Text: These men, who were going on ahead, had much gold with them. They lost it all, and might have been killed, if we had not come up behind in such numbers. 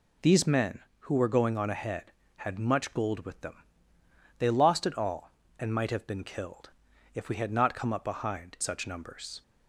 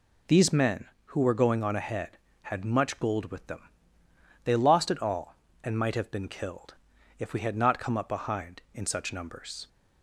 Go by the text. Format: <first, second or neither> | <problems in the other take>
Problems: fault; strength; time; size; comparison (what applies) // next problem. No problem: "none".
second | skips "in"; at 8.5 s